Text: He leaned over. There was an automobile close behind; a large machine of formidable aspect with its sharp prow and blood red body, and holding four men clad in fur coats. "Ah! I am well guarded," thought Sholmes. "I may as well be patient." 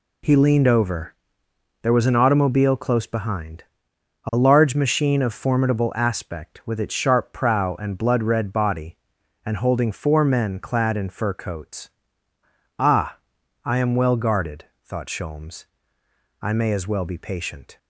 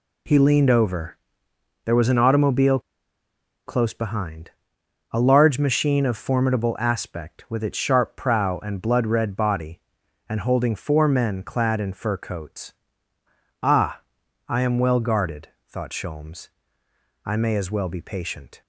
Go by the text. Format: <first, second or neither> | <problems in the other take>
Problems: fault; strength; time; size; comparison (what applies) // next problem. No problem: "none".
first | pauses between "automobile" and "close"; noticeable; at 2.7 s; 0.87 s long